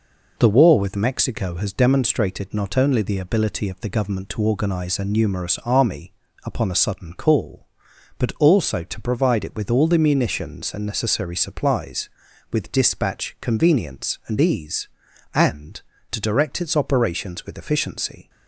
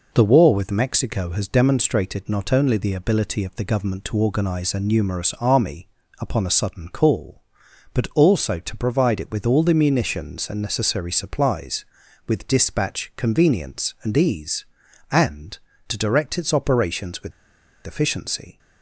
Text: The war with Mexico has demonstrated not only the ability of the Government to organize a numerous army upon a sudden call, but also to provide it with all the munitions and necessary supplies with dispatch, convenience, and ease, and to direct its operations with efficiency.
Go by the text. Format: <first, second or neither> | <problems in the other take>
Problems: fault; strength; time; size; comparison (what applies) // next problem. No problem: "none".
first | pauses between "army" and "upon"; slight; at 5.8 s; 0.32 s long; slight in the first // pauses between "with" and "efficiency"; noticeable; at 17.3 s; 0.54 s long